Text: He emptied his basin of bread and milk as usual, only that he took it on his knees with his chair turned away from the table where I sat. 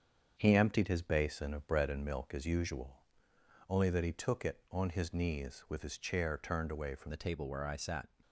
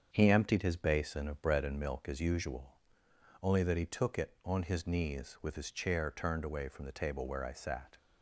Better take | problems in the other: second | starts louder than the rest; strong; until 1.3 s; 7 dB; strong in the second // changes voice at "the"; from 7.0 s on; 1.0 s long

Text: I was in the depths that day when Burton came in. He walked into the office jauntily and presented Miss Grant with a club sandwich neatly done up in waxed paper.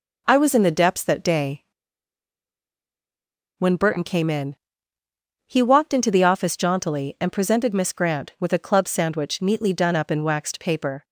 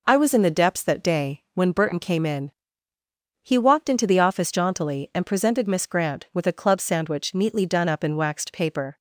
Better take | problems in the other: second | pauses between "day" and "when"; strong; at 1.6 s; 1.9 s long

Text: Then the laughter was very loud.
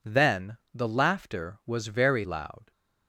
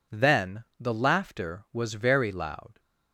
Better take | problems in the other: neither | pauses between "Then" and "the"; slight; the same in both

